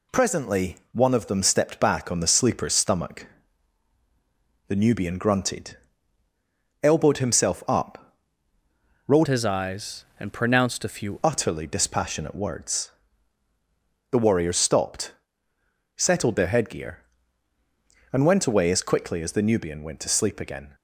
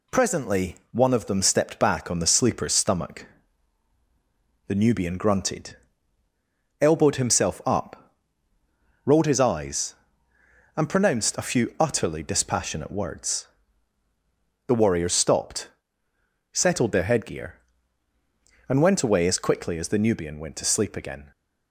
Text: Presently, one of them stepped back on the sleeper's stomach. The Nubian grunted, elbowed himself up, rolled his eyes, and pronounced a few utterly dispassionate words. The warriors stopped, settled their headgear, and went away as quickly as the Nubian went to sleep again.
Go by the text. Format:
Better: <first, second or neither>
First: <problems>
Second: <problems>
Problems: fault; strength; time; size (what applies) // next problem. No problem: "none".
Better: second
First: changes voice from "his" to "few"; from 9.2 to 11.1 s; 1.9 s long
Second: none